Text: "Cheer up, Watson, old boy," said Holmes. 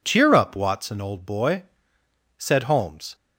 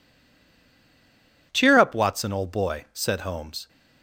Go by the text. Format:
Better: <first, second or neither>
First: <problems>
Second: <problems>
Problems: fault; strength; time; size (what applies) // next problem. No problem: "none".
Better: first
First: none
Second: stays silent before the first word; noticeable; until 1.5 s; 1.5 s long